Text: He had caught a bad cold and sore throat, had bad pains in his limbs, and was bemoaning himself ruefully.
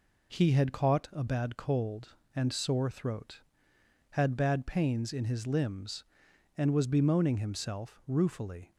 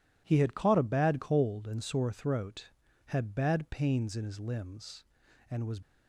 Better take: first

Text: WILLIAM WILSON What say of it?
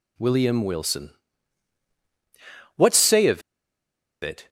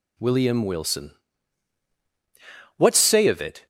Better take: second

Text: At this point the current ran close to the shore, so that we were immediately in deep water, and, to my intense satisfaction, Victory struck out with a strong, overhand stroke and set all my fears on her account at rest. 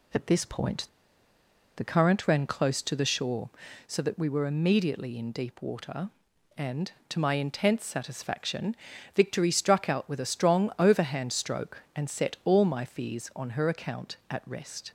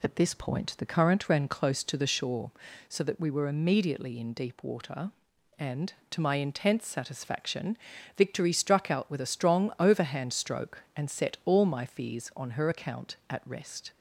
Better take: second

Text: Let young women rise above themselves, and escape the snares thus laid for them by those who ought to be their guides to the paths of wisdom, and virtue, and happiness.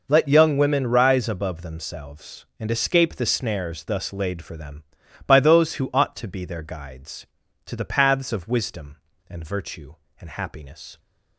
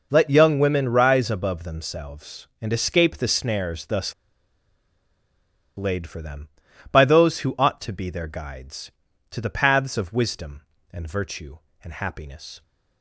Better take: first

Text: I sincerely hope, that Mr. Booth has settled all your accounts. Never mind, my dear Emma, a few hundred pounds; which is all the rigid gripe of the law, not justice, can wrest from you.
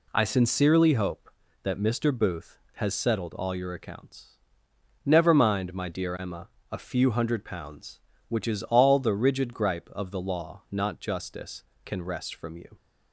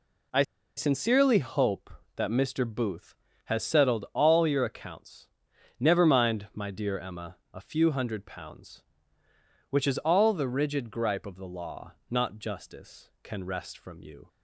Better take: first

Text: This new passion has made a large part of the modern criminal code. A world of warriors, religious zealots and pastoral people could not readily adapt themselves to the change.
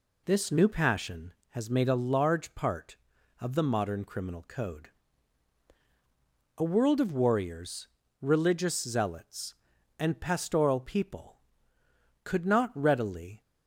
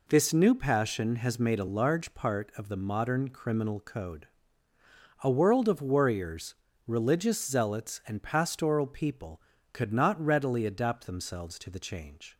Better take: second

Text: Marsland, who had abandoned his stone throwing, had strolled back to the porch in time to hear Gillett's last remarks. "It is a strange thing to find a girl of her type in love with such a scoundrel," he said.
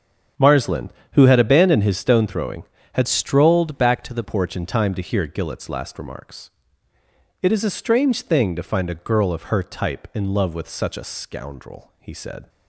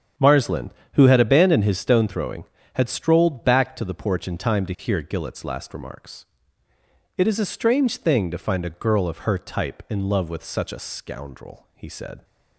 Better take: second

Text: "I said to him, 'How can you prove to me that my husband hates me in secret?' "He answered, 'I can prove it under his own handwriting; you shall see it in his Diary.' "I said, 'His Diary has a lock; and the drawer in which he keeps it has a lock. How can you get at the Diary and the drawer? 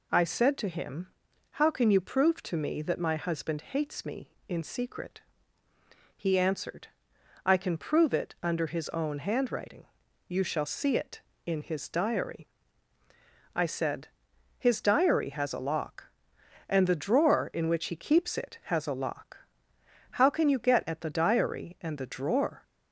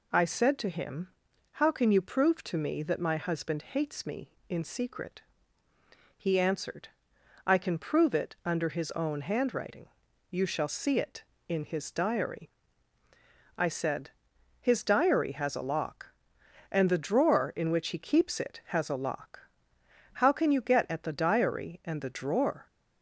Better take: neither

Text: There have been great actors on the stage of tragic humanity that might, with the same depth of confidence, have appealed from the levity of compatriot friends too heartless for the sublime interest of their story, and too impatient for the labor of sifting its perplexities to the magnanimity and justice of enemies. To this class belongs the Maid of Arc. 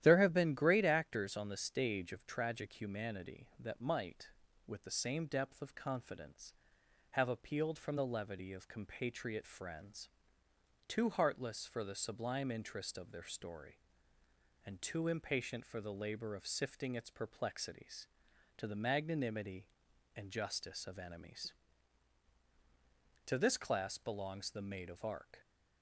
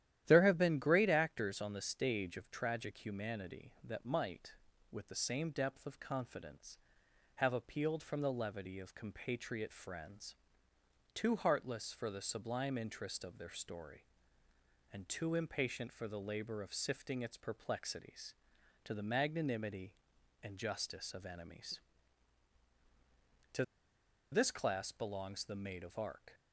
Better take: first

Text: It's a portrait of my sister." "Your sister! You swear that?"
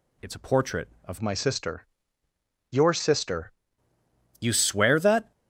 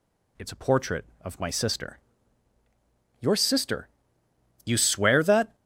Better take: second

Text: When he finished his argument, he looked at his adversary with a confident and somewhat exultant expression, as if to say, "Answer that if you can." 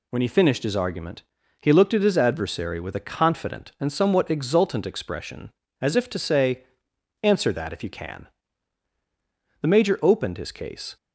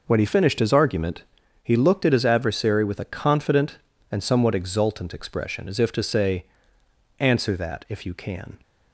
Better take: second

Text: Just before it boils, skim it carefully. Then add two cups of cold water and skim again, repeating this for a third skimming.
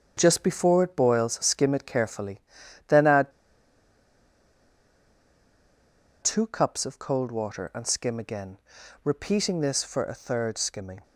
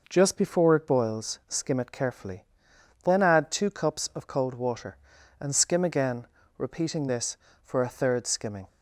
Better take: second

